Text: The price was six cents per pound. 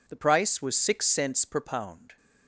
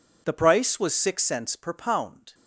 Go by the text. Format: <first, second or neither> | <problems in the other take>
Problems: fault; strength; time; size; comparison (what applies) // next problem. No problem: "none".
neither | none